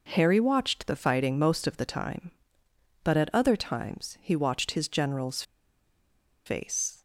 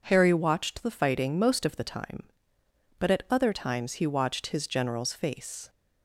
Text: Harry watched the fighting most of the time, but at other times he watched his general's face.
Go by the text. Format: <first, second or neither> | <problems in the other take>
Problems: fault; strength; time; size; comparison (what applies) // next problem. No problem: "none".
second | pauses between "general's" and "face"; at 5.4 s; 1.0 s long